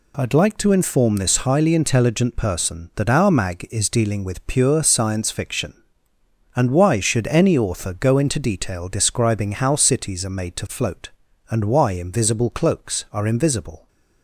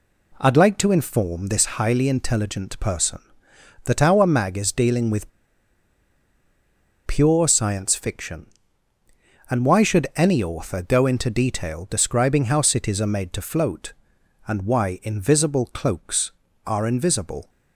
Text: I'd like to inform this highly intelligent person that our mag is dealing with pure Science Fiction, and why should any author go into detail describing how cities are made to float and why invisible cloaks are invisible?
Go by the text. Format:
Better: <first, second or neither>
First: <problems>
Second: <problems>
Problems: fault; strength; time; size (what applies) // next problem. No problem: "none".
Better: first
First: none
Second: pauses between "with" and "pure"; strong; at 5.3 s; 1.7 s long